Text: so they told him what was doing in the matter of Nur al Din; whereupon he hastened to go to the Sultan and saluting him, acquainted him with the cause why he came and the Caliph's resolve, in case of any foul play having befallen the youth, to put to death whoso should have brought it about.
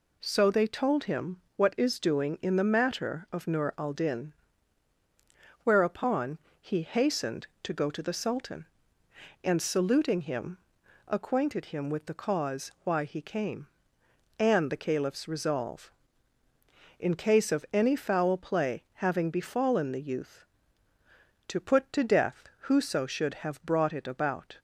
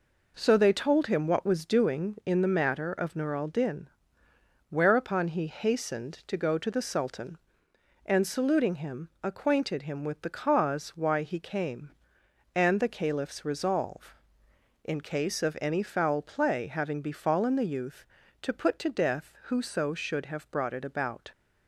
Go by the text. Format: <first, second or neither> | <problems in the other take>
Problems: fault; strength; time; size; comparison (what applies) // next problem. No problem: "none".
second | pauses between "him" and "what"; slight; at 1.3 s; 0.20 s long // says "is" for "was"; at 1.7 s // pauses between "whereupon" and "he"; slight; at 6.3 s; 0.22 s long // pauses between "death" and "whoso"; slight; at 22.4 s; 0.16 s long